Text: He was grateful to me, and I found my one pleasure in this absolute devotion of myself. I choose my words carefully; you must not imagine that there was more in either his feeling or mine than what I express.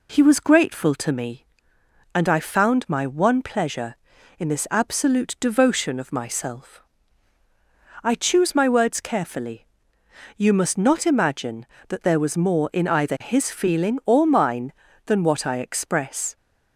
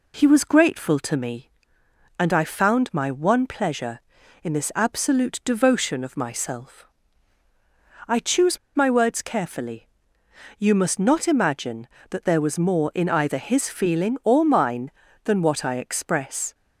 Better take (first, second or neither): first